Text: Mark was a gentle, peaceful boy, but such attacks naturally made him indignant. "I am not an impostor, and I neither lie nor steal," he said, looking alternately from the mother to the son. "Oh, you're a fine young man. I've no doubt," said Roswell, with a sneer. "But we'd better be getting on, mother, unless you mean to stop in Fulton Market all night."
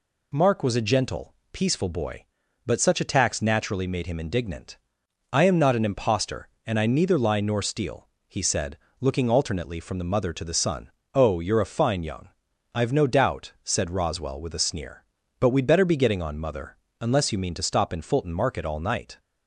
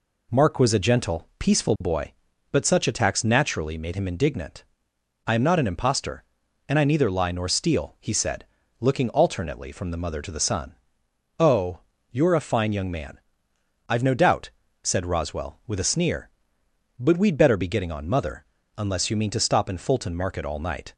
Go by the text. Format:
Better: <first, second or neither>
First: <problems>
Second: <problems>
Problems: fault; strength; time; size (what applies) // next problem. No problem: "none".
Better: second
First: skips "man"; at 12.5 s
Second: none